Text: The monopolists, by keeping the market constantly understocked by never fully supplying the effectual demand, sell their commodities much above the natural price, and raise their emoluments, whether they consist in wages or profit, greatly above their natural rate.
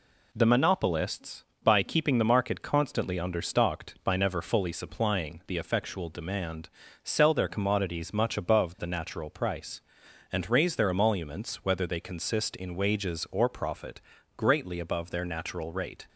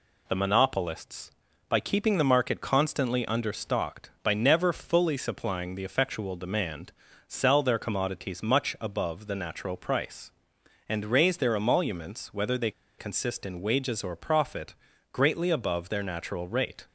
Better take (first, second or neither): first